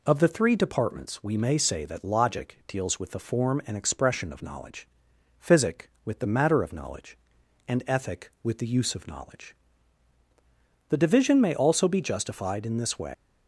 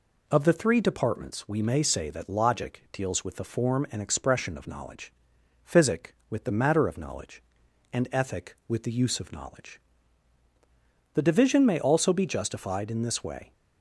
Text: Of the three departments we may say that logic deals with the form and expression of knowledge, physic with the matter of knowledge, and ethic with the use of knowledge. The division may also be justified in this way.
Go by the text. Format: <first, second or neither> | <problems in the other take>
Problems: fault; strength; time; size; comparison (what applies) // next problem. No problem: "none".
second | leaves "way" unfinished; at 13.1 s; 125 ms